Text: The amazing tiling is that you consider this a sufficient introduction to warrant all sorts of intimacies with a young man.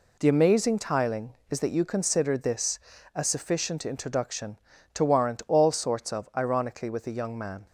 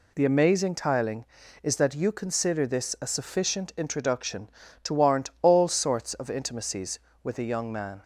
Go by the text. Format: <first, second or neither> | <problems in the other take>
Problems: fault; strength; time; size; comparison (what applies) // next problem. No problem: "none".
second | pauses between "this" and "a"; slight; at 2.7 s; 0.34 s long // says "ironically" for "intimacies"; at 6.3 s